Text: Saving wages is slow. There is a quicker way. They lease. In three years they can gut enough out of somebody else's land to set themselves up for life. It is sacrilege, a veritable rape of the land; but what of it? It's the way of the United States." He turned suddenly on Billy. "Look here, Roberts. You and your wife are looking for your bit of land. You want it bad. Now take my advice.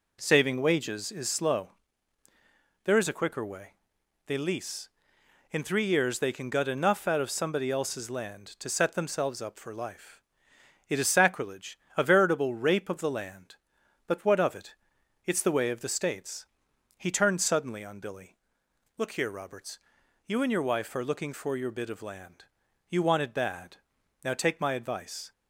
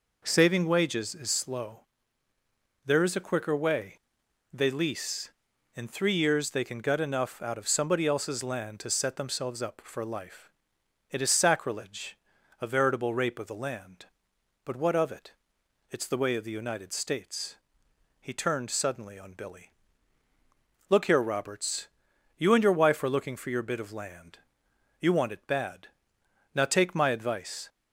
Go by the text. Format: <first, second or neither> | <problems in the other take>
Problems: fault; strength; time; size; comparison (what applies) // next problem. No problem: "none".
second | skips "United"; at 15.8 s